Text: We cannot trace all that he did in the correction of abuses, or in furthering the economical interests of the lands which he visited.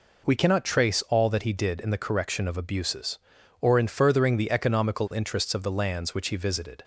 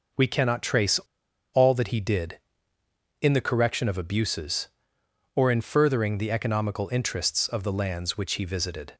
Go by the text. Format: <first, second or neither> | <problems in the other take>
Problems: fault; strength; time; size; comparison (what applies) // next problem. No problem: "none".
first | pauses between "trace" and "all"; noticeable; at 0.9 s; 0.55 s long